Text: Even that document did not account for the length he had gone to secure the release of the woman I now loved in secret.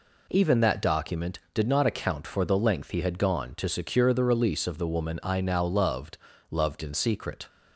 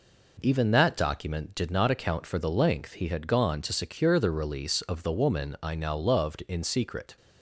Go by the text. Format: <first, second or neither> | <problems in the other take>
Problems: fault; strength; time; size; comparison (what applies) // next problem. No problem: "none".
second | says "loved" twice; at 6.4 s